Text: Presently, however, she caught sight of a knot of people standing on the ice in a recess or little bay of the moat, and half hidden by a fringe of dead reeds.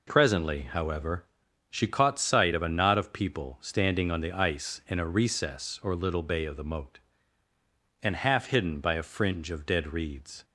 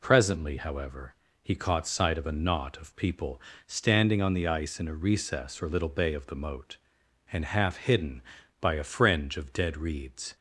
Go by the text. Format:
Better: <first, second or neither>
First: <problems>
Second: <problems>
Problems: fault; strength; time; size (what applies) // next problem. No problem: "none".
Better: first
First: none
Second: says "he" for "she"; at 1.4 s // pauses between "people" and "standing"; slight; at 3.4 s; 0.26 s long